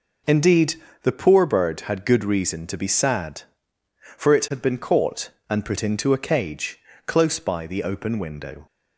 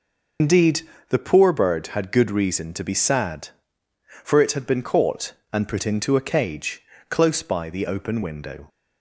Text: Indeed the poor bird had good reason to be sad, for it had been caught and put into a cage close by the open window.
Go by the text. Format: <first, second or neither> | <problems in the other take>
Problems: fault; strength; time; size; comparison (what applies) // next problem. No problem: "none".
first | loses the start of "Indeed"; at 0.3 s; 75 ms // pauses between "Indeed" and "the"; slight; at 0.8 s; 0.26 s long; slight in the first // pauses between "cage" and "close"; slight; at 6.8 s; 0.26 s long; slight in the first